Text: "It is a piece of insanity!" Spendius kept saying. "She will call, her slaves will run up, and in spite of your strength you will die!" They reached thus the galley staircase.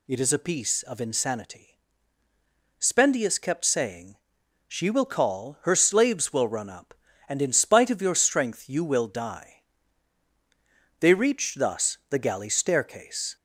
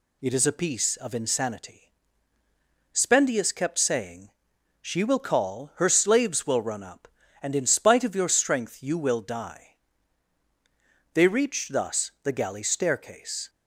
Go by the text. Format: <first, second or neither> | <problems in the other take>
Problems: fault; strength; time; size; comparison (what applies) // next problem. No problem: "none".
second | gets louder; slight; throughout; 2.5 dB